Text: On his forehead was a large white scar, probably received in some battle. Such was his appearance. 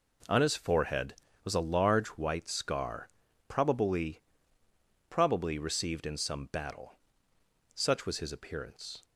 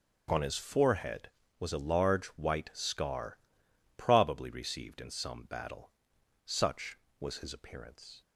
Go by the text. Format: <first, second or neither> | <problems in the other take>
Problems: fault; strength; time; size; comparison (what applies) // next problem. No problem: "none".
second | says "probably" twice; at 5.0 s